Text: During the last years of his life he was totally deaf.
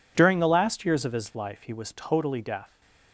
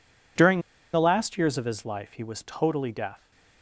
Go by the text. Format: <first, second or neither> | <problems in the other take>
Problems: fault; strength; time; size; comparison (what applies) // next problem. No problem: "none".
first | pauses between "During" and "the"; slight; at 0.6 s; 0.32 s long